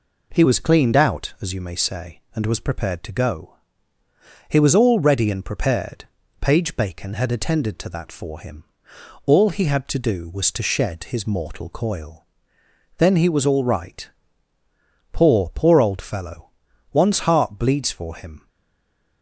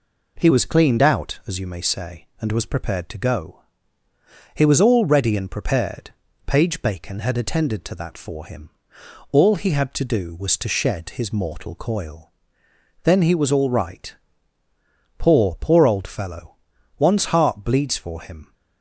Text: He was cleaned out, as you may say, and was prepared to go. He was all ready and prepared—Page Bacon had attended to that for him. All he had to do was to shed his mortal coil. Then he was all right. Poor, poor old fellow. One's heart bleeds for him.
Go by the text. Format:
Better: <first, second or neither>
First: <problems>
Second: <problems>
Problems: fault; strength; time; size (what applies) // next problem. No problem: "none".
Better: second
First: stays silent after the last word; slight; from 18.4 s on; 0.8 s long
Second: none